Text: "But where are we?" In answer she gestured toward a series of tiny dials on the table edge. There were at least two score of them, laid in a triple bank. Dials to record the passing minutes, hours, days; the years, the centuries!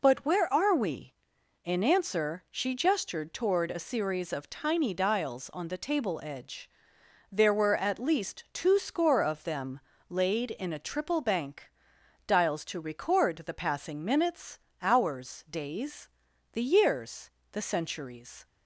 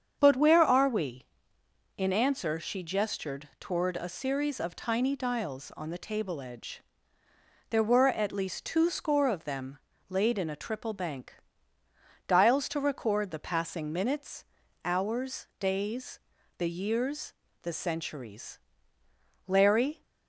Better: first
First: none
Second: starts louder than the rest; strong; until 1.2 s; 7.5 dB // goes on to say "Larry"; from 19.4 s on; 0.54 s long

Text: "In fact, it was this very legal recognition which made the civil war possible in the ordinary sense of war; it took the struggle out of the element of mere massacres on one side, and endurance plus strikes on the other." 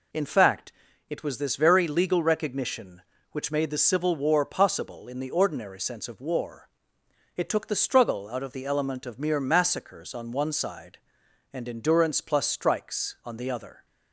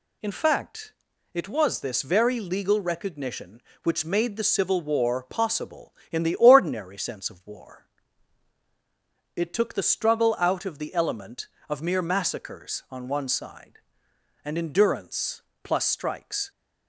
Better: first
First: none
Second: pauses between "endurance" and "plus"; slight; at 15.4 s; 0.20 s long // stops before "on the other"; at 16.5 s

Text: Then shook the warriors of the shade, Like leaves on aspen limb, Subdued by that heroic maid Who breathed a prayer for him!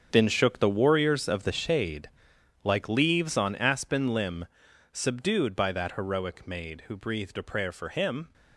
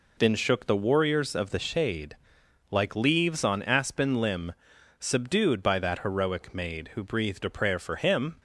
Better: second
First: gets quieter; strong; throughout; 13 dB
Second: none

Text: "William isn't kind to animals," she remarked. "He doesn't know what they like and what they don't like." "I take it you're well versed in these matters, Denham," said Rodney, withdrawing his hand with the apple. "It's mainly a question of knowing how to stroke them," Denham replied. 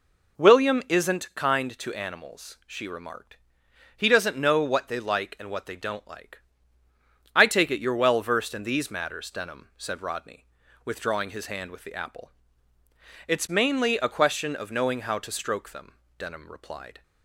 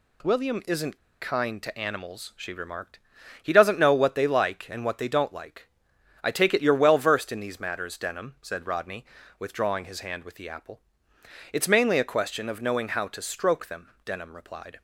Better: first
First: none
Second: pauses between "isn't" and "kind"; slight; at 0.9 s; 0.22 s long

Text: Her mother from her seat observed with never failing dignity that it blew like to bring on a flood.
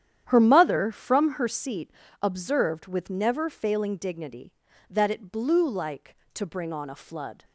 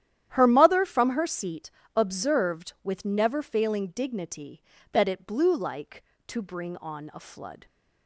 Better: neither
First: starts louder than the rest; strong; until 1.2 s; 10 dB // pauses between "seat" and "observed"; slight; at 1.9 s; 0.28 s long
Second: starts louder than the rest; strong; until 1.3 s; 11.5 dB // pauses between "seat" and "observed"; slight; at 1.7 s; 0.26 s long

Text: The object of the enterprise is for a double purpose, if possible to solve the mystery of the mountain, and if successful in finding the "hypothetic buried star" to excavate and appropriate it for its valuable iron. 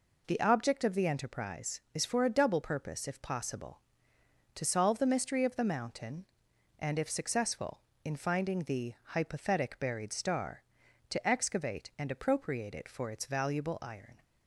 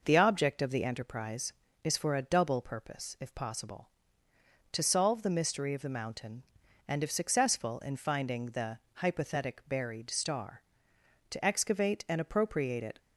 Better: first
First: none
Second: pauses between "the" and "hypothetic"; slight; at 8.7 s; 0.16 s long // stops before "for its valuable iron"; at 12.9 s

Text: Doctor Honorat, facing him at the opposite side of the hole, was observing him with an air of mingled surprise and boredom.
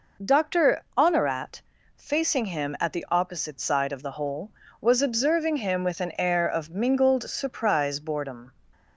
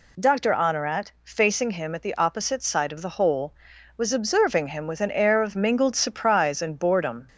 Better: second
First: pauses between "Doctor" and "Honorat"; slight; at 0.8 s; 0.16 s long // skips "and"; at 7.9 s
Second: none

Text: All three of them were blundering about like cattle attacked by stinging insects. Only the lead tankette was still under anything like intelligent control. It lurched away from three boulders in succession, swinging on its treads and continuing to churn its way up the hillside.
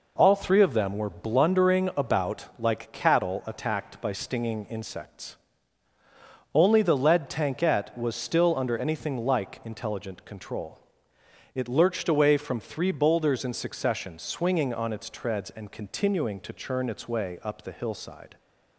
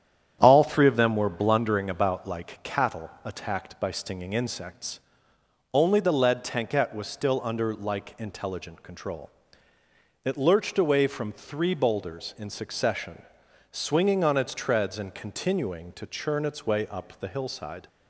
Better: first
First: none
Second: starts louder than the rest; strong; until 1.4 s; 9.5 dB // pauses between "cattle" and "attacked"; slight; at 3.0 s; 0.16 s long // skips "anything"; at 7.7 s

